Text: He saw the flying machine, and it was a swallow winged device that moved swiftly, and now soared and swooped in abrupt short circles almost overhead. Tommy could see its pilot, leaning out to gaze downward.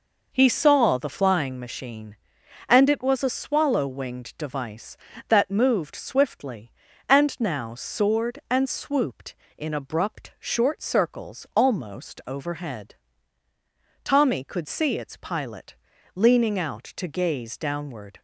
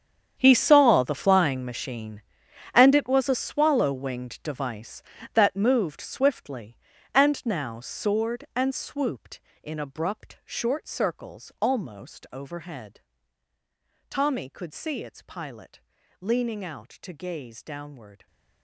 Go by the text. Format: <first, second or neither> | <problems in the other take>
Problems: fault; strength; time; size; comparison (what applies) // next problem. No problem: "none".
first | gets quieter; strong; throughout; 16 dB